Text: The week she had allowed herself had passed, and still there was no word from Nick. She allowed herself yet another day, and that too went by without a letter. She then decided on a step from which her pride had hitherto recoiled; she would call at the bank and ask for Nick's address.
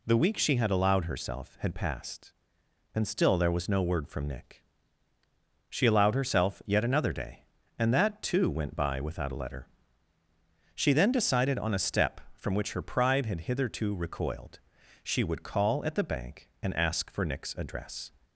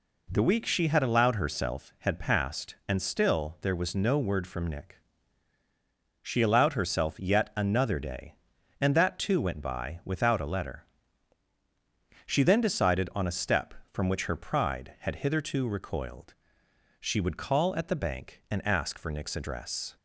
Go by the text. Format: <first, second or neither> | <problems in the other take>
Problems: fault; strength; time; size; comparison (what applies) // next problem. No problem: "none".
neither | none